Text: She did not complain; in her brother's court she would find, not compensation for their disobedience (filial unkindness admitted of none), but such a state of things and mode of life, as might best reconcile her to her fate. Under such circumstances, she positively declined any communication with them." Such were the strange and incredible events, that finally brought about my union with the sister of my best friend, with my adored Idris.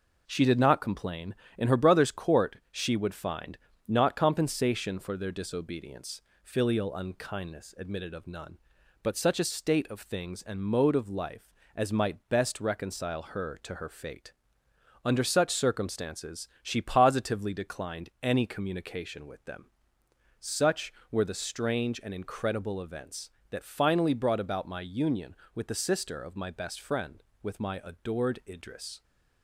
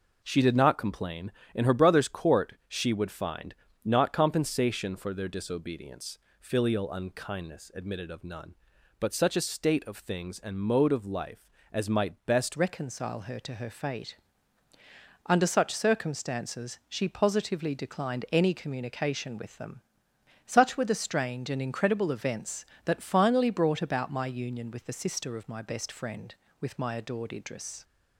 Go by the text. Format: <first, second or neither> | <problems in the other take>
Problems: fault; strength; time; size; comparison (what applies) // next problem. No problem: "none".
first | pauses between "court" and "she"; slight; at 2.5 s; 0.16 s long; slight in the first // changes voice at "reconcile"; from 12.5 s on; 15.3 s long